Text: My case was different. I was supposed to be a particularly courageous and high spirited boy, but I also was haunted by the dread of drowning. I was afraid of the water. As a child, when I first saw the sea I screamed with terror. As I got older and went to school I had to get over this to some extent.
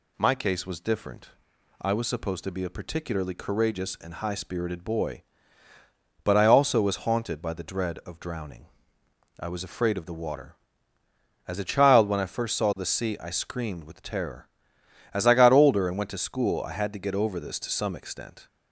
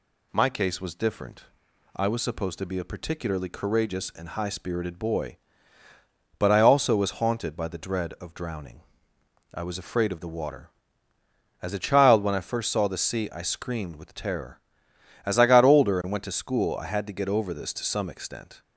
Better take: neither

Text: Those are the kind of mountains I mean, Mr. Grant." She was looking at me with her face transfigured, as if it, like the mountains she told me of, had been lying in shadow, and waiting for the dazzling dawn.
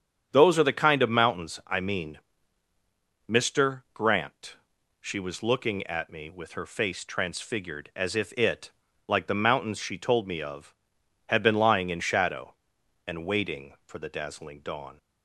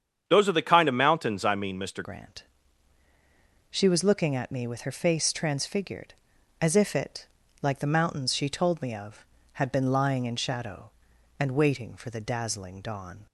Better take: first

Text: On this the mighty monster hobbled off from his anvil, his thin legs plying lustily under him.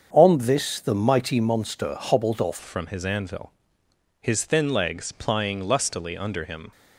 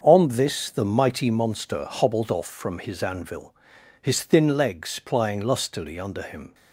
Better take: second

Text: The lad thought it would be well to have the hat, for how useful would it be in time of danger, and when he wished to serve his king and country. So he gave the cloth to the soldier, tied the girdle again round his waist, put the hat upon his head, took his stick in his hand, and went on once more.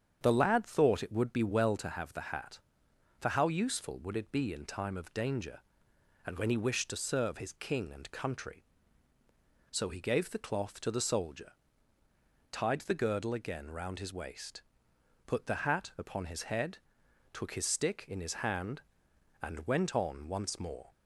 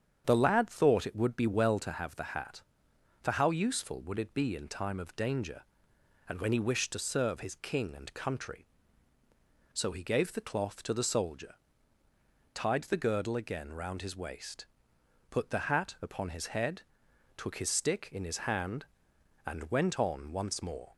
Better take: neither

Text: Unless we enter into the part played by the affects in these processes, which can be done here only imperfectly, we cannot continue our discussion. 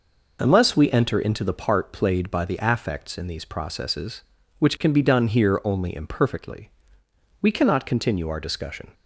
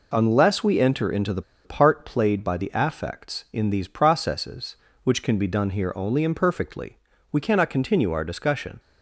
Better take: first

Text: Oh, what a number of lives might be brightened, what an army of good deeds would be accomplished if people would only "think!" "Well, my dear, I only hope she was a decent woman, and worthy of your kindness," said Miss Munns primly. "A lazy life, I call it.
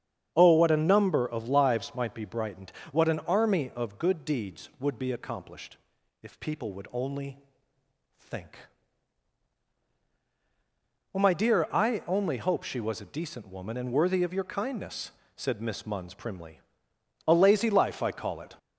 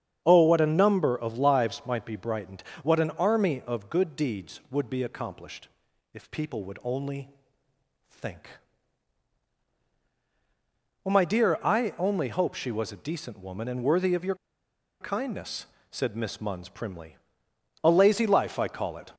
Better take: first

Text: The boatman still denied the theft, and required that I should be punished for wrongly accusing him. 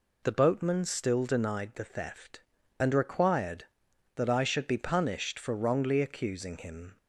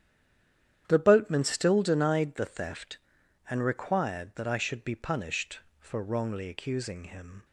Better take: first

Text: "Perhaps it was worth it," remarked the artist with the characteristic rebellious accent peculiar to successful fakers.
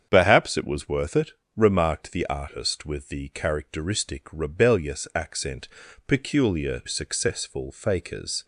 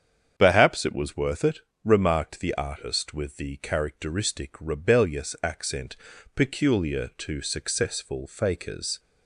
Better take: second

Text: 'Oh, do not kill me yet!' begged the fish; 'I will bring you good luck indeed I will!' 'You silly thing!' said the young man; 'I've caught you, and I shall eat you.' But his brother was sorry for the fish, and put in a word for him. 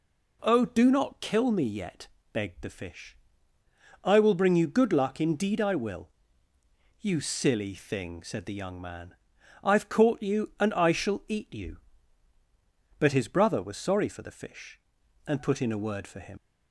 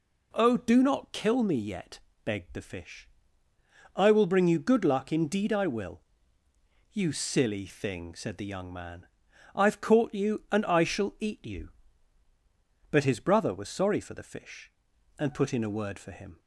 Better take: second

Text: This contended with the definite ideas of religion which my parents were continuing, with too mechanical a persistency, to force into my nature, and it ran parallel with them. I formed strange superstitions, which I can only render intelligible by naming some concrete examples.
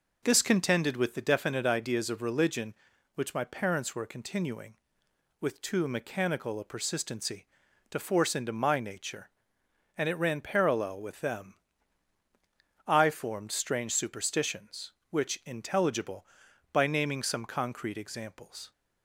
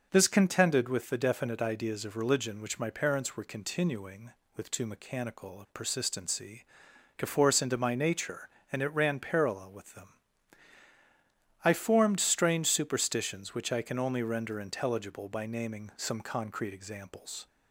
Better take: second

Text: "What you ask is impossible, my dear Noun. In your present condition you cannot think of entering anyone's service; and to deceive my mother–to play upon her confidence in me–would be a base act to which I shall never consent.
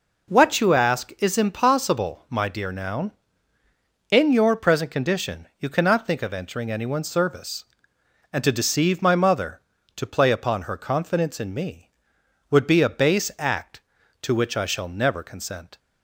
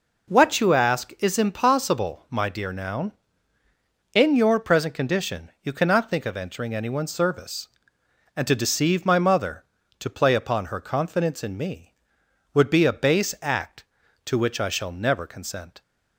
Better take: neither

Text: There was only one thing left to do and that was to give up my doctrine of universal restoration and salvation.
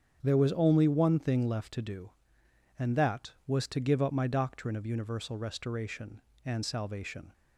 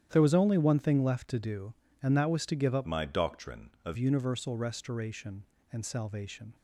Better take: first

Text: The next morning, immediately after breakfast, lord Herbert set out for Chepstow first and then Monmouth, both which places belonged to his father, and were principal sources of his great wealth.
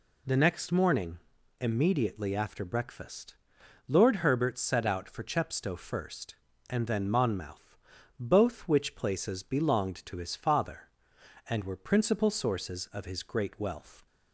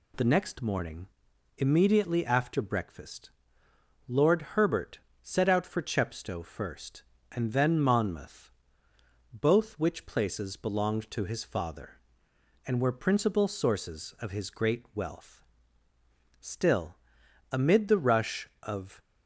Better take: first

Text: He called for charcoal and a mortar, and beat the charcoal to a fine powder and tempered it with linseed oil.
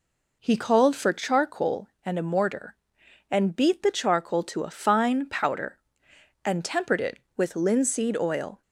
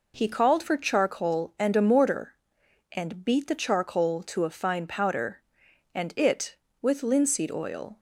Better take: first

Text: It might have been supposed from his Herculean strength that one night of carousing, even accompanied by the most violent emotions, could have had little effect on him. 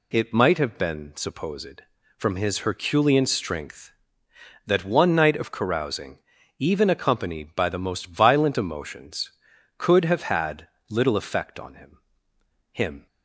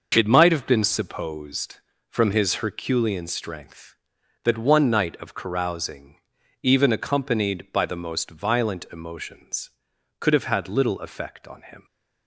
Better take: second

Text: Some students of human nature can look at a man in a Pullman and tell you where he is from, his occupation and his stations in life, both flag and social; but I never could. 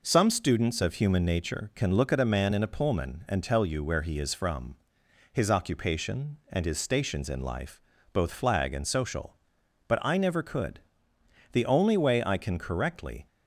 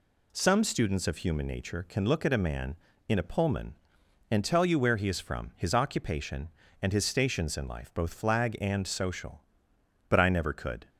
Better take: second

